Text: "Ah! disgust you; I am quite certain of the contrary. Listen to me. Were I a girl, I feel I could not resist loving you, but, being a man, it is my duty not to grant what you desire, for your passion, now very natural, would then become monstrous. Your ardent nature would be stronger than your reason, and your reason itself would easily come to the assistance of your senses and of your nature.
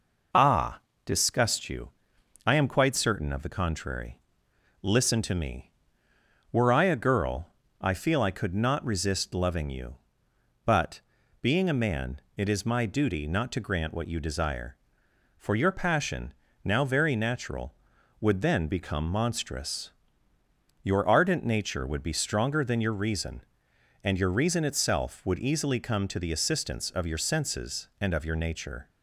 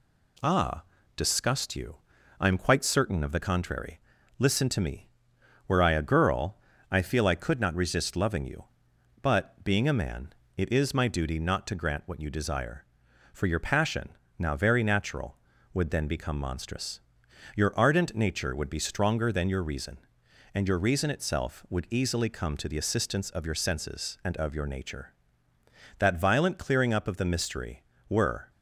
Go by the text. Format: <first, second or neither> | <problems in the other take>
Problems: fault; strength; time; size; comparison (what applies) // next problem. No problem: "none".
first | goes on to say "That violent clearing up of the mystery were"; strong; from 25.9 s on; 2.5 s long